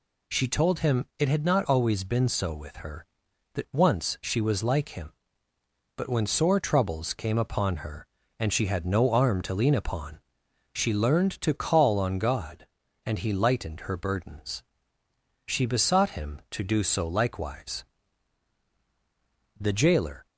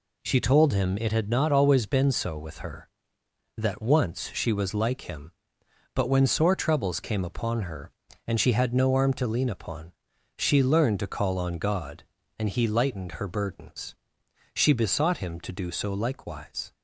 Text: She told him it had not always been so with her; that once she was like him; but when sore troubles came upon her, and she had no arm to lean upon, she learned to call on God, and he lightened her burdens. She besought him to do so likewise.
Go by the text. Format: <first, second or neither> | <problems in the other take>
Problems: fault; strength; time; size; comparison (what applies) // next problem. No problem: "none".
second | goes on to say "The jailer"; noticeable; from 19.5 s on; 0.66 s long